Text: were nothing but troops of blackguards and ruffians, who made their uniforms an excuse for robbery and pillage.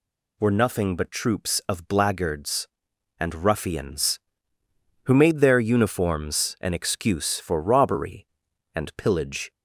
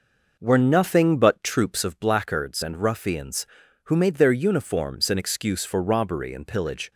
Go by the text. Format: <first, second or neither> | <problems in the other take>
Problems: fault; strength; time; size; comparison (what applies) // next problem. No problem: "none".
first | starts louder than the rest; noticeable; until 2.0 s; 5.5 dB